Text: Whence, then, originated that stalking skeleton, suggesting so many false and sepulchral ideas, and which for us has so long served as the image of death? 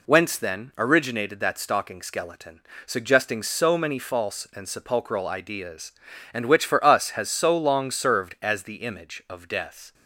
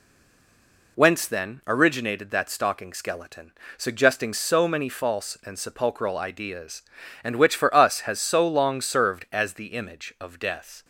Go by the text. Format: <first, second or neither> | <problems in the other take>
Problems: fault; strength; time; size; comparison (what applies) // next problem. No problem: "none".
first | stays silent before the first word; slight; until 0.9 s; 0.9 s long